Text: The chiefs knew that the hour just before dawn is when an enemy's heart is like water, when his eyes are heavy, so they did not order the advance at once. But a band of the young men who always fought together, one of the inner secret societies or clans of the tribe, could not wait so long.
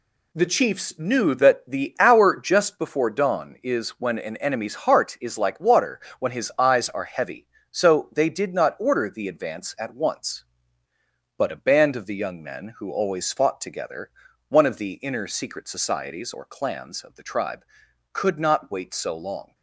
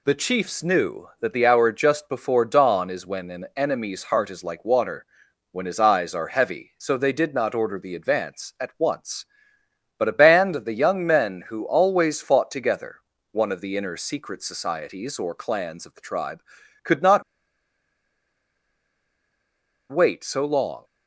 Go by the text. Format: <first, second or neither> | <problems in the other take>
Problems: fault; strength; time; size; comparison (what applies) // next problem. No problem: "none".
first | pauses between "not" and "wait"; strong; at 17.2 s; 2.6 s long